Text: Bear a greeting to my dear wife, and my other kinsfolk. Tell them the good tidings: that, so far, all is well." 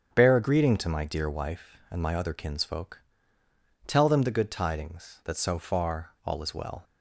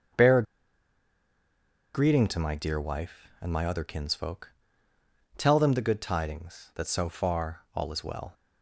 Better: first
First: starts louder than the rest; strong; until 1.1 s; 7.5 dB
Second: starts louder than the rest; strong; until 2.6 s; 8 dB // pauses between "a" and "greeting"; strong; at 0.4 s; 1.5 s long

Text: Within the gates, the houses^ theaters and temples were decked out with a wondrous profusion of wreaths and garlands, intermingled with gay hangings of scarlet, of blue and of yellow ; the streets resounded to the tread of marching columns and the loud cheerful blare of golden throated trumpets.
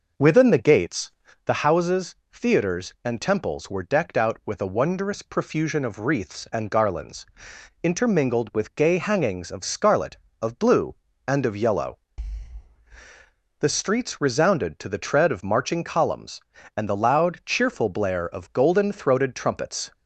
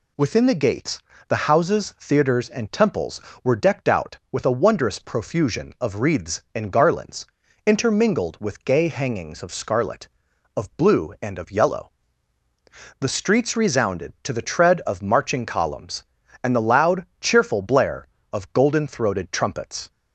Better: second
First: starts louder than the rest; noticeable; until 1.4 s; 5.5 dB // pauses between "houses" and "theaters"; slight; at 2.1 s; 0.16 s long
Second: none

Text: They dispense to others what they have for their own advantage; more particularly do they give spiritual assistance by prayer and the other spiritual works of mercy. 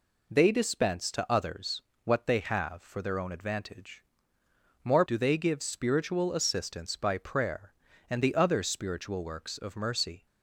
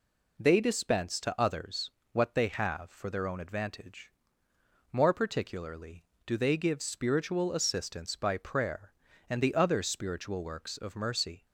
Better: second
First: pauses between "others" and "what"; slight; at 1.8 s; 0.22 s long // skips "particularly"; at 5.0 s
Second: pauses between "others" and "what"; slight; at 1.8 s; 0.21 s long

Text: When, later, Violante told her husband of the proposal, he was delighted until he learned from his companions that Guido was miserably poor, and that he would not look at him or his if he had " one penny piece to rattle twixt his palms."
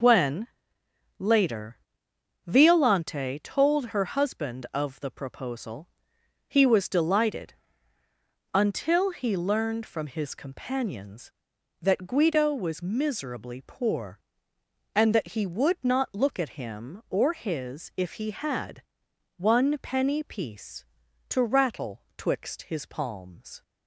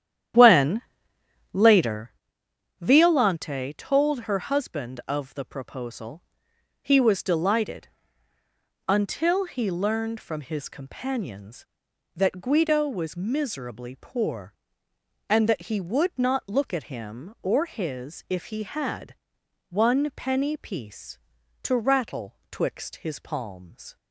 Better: first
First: pauses between "delighted" and "until"; noticeable; at 7.5 s; 0.98 s long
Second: starts louder than the rest; strong; until 2.1 s; 10.5 dB // pauses between "delighted" and "until"; noticeable; at 7.8 s; 0.98 s long

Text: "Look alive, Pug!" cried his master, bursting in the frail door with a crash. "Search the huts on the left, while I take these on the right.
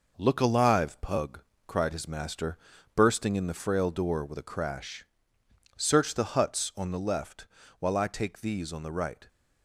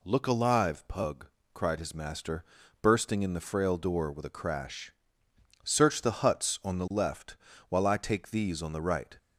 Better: second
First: gets quieter; noticeable; throughout; 5 dB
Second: none

